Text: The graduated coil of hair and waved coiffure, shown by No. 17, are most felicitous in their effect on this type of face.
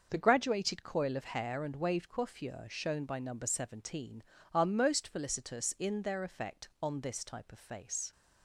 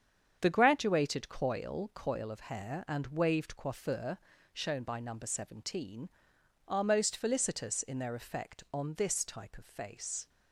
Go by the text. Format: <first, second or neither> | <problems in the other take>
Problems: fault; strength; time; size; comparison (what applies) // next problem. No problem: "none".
first | starts louder than the rest; strong; until 1.4 s; 7.5 dB; also in the first // says "coil" twice; at 1.9 s